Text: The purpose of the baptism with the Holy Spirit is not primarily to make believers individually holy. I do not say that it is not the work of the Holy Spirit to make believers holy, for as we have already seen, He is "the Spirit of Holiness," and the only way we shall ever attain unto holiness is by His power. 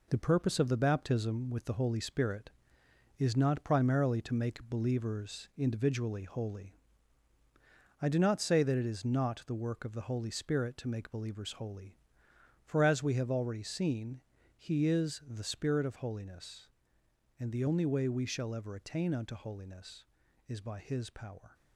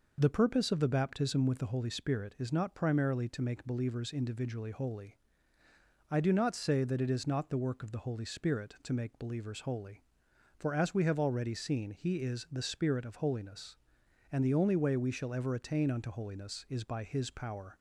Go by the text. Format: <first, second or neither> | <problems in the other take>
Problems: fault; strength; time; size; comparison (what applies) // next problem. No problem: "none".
second | gets quieter; throughout; 6.5 dB